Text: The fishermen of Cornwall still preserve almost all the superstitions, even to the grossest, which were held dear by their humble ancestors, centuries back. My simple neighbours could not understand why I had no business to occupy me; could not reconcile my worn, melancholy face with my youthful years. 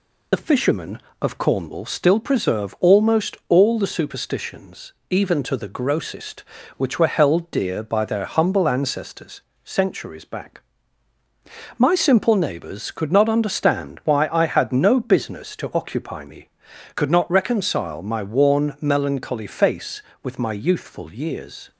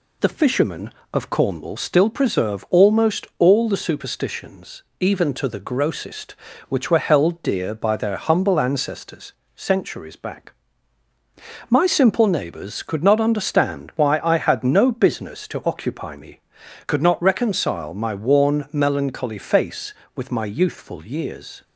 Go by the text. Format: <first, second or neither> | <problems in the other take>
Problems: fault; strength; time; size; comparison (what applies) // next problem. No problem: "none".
second | loses the start of "The"; at 0.3 s; 40 ms